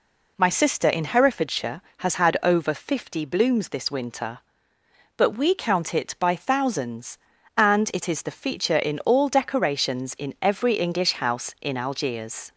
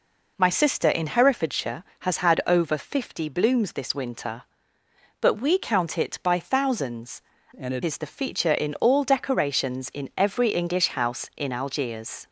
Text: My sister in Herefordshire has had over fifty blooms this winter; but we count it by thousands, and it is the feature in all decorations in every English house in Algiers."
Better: first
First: none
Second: changes voice from "and" to "it"; from 7.5 to 7.8 s; 0.3 s long

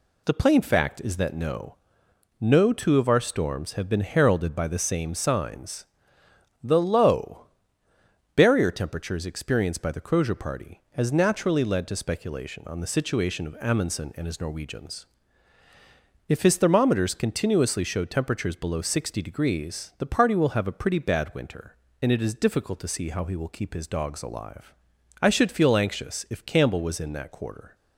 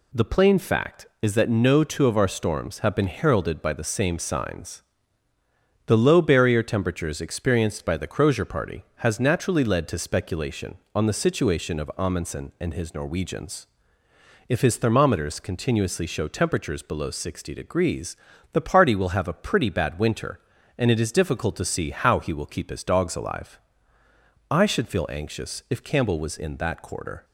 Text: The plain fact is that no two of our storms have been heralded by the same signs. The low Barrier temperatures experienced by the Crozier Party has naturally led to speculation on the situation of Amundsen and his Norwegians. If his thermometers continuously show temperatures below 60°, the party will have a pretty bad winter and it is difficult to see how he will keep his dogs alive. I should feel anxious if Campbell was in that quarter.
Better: second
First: says "no" twice; at 2.4 s // pauses between "low" and "Barrier"; noticeable; at 7.4 s; 0.88 s long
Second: none

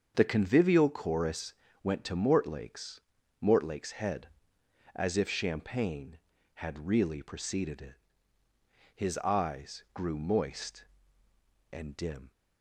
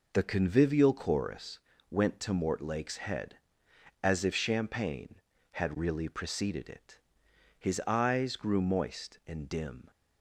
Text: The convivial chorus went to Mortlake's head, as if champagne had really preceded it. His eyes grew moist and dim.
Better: second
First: starts louder than the rest; until 1.1 s; 7 dB // pauses between "chorus" and "went"; slight; at 1.5 s; 0.32 s long // says "Mortlake's" twice; at 3.4 s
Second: pauses between "chorus" and "went"; slight; at 1.5 s; 0.32 s long

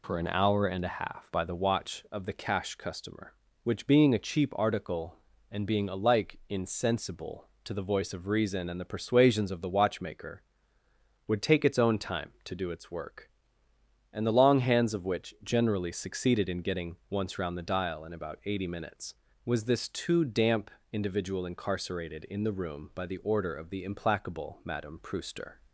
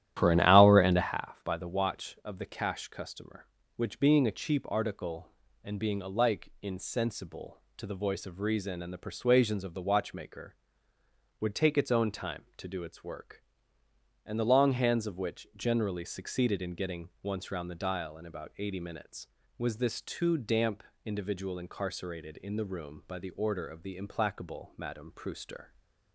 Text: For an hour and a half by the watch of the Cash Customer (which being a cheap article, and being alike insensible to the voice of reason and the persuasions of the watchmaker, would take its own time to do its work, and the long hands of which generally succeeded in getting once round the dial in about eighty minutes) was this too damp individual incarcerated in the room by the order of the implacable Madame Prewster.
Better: first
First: pauses between "damp" and "individual"; slight; at 20.6 s; 0.24 s long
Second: starts louder than the rest; strong; until 1.3 s; 12.5 dB // pauses between "damp" and "individual"; slight; at 20.8 s; 0.24 s long

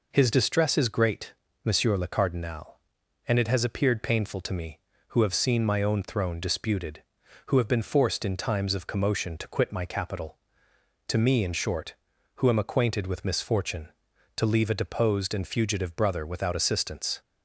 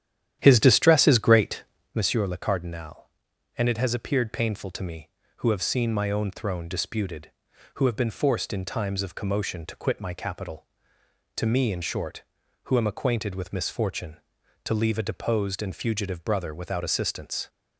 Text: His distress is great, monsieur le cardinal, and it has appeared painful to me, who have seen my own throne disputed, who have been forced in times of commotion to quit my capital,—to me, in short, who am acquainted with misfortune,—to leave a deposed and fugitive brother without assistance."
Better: first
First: none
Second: starts louder than the rest; strong; until 2.0 s; 11 dB

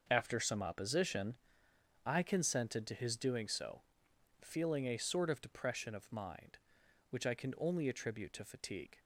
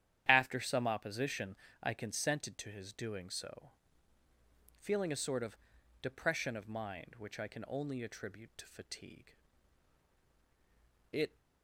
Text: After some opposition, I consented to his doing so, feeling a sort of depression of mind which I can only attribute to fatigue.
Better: first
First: starts louder than the rest; noticeable; until 1.1 s; 6 dB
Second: starts louder than the rest; strong; until 1.2 s; 10.5 dB // pauses between "of" and "depression"; noticeable; at 5.5 s; 0.46 s long // goes on to say "It"; slight; from 11.1 s on; 0.26 s long

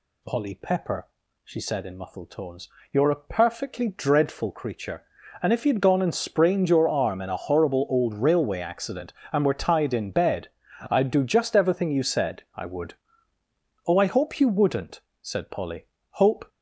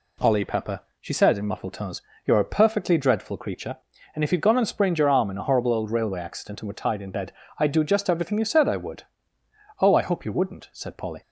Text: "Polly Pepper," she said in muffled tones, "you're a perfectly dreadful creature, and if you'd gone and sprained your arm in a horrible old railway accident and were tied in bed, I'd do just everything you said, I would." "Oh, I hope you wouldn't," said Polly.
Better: second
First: goes on to say "Hope"; slight; from 16.1 s on; 0.38 s long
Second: none

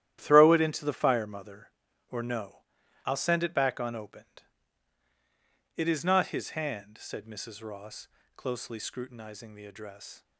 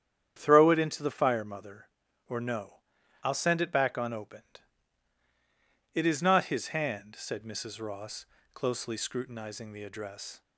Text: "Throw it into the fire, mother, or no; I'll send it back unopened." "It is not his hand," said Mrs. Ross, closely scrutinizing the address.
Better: second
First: gets quieter; strong; throughout; 10.5 dB // starts louder than the rest; strong; until 1.2 s; 12 dB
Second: starts louder than the rest; strong; until 1.3 s; 9.5 dB

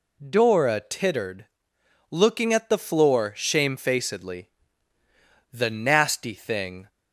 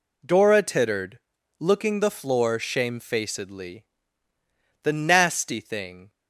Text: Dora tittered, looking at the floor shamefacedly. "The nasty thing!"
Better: first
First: none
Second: skips "at"; at 1.9 s

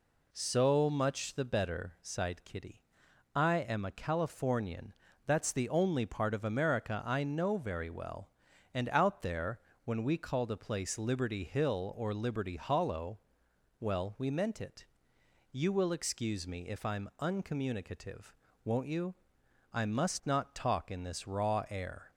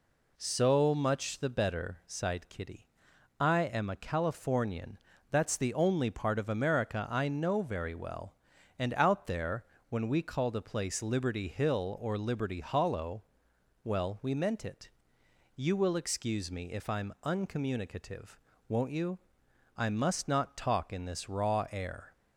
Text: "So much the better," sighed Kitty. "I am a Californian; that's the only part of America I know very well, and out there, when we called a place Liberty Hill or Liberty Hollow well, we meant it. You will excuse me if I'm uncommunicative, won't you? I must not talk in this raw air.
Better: neither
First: pauses between "Hollow" and "well"; noticeable; at 13.1 s; 0.62 s long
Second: pauses between "Hollow" and "well"; noticeable; at 13.2 s; 0.62 s long

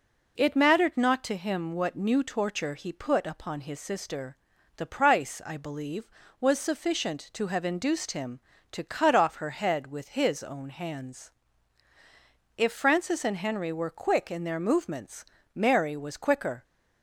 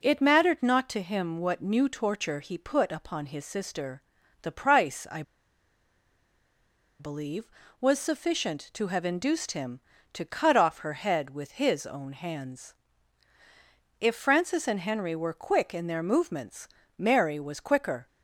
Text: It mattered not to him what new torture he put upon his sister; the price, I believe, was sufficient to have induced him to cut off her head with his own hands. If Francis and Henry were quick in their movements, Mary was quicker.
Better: first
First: none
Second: pauses between "I" and "believe"; strong; at 5.2 s; 1.7 s long

